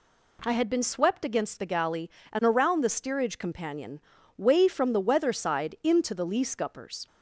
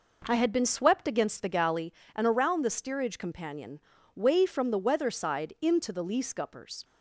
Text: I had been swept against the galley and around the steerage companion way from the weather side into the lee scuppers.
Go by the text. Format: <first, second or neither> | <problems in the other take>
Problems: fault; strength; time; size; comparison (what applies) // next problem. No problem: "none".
first | starts louder than the rest; noticeable; until 1.9 s; 5 dB // pauses between "companion" and "way"; slight; at 3.7 s; 0.34 s long; slight in the first